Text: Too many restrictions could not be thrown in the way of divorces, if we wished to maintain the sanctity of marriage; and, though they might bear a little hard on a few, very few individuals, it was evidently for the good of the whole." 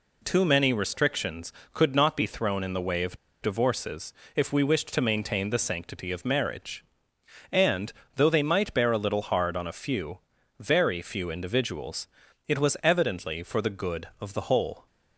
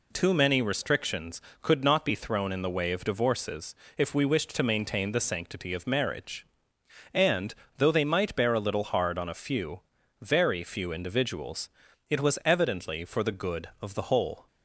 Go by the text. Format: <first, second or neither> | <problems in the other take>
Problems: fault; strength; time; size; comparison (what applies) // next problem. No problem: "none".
second | pauses between "of" and "divorces"; slight; at 3.1 s; 0.25 s long